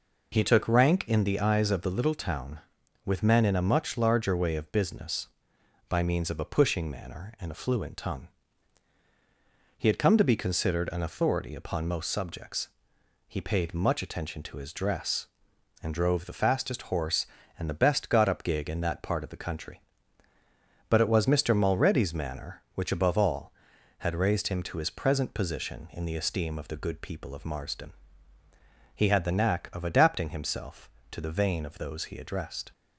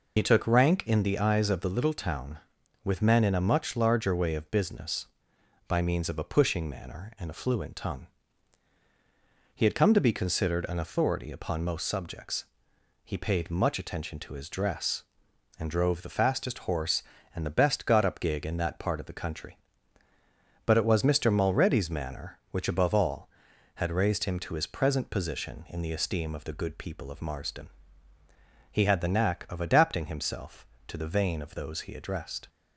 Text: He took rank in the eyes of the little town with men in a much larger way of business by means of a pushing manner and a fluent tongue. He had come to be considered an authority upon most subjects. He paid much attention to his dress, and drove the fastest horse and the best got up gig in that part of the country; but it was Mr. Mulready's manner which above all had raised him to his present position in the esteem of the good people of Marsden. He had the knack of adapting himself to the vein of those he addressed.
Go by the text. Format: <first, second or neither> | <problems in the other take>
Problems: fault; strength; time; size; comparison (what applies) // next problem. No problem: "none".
first | loses the start of "He"; at 0.1 s; 55 ms